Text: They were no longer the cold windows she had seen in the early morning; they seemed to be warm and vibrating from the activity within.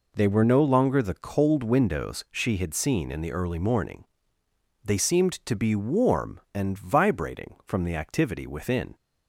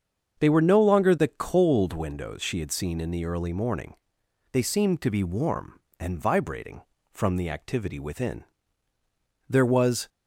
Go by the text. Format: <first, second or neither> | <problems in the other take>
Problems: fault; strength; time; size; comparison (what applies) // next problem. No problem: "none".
first | starts louder than the rest; strong; until 1.4 s; 7 dB // goes on to say "There was"; from 9.4 s on; 0.60 s long